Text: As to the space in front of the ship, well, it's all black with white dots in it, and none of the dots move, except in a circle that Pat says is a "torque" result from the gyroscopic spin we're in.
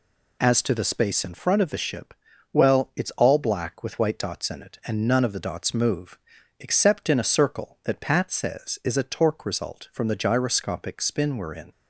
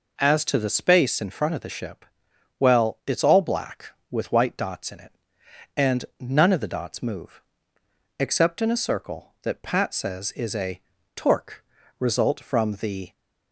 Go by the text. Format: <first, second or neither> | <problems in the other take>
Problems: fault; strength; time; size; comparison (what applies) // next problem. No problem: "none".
first | pauses between "a" and "torque"; at 10.7 s; 0.38 s long // pauses between "torque" and "result"; at 11.6 s; 0.38 s long // stops before "gyroscopic spin we're in"; at 13.1 s